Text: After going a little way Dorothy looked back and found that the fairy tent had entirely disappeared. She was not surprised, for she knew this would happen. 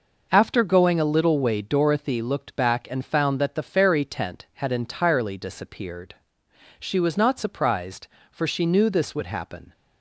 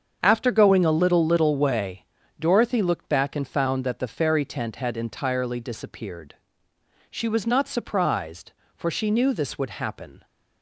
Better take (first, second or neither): first